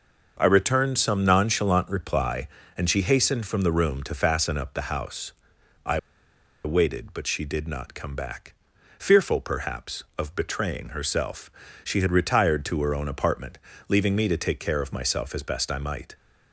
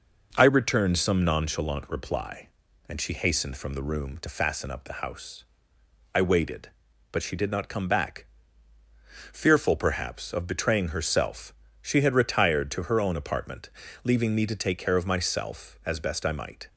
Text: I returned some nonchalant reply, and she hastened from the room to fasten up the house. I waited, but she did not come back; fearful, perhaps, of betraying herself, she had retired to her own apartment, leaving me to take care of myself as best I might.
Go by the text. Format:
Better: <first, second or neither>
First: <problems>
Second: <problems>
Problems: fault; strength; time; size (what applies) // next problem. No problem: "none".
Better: second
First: starts louder than the rest; until 1.4 s; 6 dB // pauses between "I" and "waited"; noticeable; at 5.9 s; 0.66 s long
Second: none